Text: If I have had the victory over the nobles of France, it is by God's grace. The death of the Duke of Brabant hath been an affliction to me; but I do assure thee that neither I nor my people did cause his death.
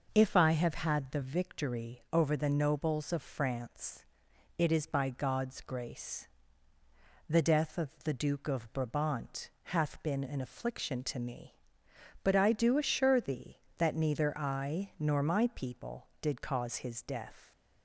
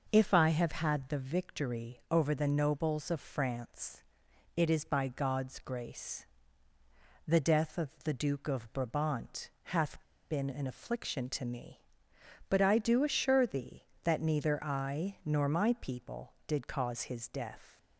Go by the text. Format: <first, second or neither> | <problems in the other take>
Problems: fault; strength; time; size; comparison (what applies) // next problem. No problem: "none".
first | pauses between "of" and "the"; slight; at 7.8 s; 0.16 s long; slight in the first // pauses between "hath" and "been"; slight; at 10.0 s; 0.28 s long